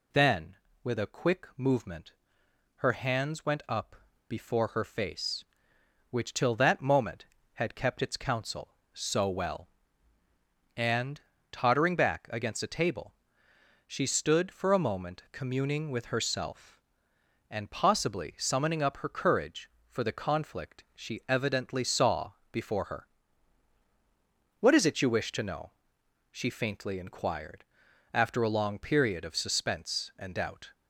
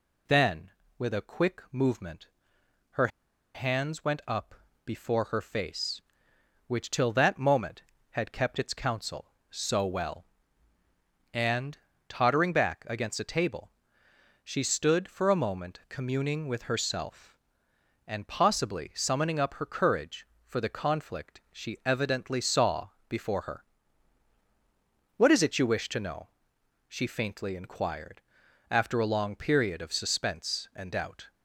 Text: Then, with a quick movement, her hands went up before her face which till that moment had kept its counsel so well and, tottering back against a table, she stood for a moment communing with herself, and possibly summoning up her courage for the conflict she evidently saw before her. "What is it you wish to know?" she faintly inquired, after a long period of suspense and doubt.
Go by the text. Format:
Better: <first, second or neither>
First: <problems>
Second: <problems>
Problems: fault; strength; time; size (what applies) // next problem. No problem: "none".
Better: first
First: pauses between "up" and "before"; slight; at 3.9 s; 0.34 s long // pauses between "saw" and "before"; slight; at 22.3 s; 0.18 s long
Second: pauses between "her" and "hands"; noticeable; at 3.0 s; 0.47 s long // pauses between "up" and "before"; slight; at 4.5 s; 0.32 s long // pauses between "saw" and "before"; slight; at 22.8 s; 0.18 s long